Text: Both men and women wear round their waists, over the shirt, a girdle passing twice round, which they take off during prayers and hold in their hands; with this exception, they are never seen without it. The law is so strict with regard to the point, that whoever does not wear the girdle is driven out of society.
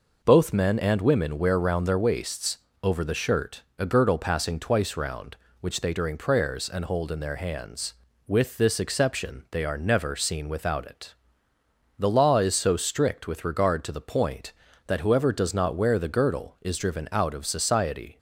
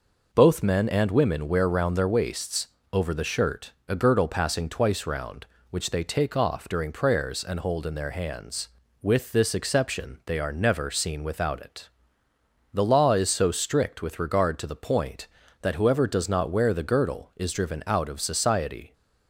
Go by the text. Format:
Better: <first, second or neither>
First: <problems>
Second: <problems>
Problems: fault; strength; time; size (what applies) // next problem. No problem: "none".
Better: second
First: skips "take off"; at 5.9 s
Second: none